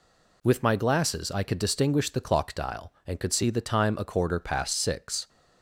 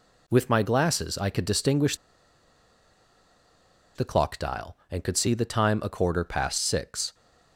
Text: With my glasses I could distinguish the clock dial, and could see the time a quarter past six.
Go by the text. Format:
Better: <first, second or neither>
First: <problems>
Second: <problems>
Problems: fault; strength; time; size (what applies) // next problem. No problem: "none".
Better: first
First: none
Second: pauses between "distinguish" and "the"; strong; at 1.9 s; 2.0 s long